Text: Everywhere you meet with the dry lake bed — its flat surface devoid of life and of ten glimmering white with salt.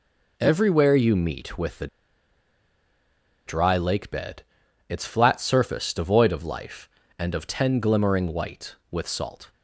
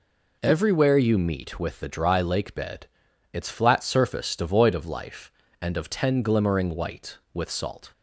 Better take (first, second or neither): second